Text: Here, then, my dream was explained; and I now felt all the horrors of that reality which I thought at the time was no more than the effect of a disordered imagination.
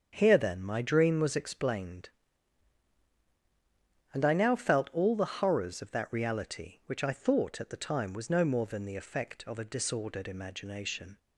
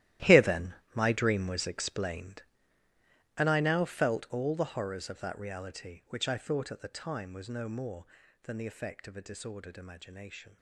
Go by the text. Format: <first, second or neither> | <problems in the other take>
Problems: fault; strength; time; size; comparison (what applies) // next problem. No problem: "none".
first | gets quieter; strong; throughout; 15.5 dB // starts louder than the rest; strong; until 1.4 s; 14 dB; strong in the first